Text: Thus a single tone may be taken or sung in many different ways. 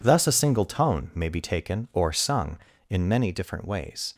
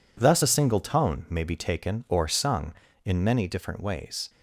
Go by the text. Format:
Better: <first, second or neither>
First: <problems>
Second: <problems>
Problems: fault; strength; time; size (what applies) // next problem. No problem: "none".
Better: neither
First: none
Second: none